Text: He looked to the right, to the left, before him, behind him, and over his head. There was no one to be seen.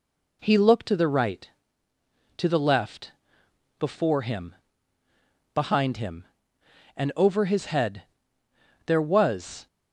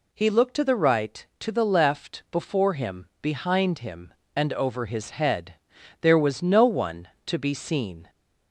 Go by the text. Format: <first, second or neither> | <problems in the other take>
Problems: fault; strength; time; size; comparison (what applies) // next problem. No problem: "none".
second | stops before "no one to be seen"; at 9.6 s